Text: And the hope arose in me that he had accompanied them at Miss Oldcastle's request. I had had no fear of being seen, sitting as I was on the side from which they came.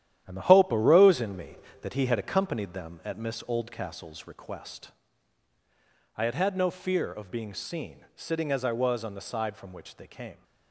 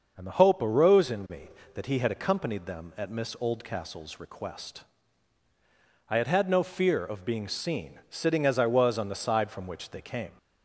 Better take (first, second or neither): second